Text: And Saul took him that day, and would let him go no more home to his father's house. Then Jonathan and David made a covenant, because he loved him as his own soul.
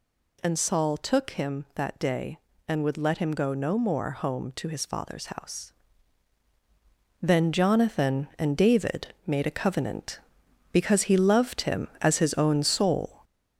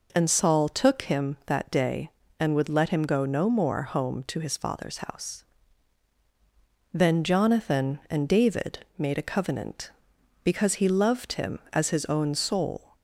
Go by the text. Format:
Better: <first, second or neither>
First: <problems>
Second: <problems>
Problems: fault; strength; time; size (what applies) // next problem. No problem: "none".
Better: second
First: gets louder; noticeable; throughout; 4 dB // pauses between "David" and "made"; slight; at 9.0 s; 0.18 s long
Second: pauses between "David" and "made"; slight; at 8.7 s; 0.18 s long